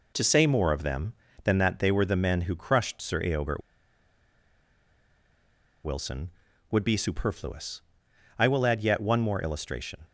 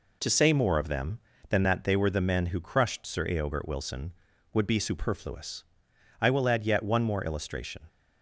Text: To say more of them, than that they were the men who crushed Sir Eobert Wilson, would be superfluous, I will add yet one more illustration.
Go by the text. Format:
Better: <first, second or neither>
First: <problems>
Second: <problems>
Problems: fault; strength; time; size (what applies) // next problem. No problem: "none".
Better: second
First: pauses between "Eobert" and "Wilson"; strong; at 3.6 s; 2.2 s long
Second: none